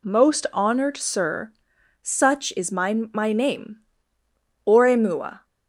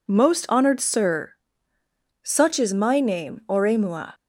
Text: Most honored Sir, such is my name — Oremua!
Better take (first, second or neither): second